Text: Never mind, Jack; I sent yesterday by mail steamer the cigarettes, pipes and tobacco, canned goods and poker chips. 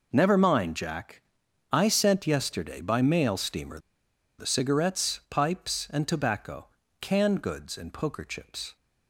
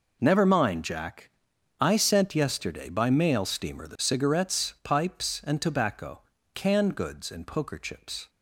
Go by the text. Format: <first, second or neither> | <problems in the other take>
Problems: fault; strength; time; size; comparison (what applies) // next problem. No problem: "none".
second | pauses between "steamer" and "the"; noticeable; at 3.7 s; 0.60 s long